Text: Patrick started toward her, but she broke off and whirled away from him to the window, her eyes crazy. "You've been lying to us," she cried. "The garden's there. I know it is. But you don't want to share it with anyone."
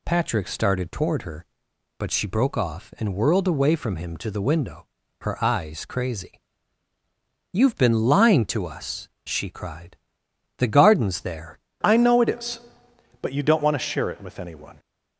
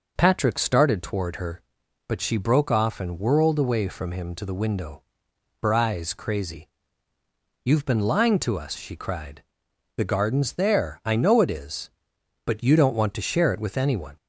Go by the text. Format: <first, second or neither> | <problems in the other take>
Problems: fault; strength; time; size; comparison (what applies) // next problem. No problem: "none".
second | changes voice at "I"; from 11.8 s on; 2.9 s long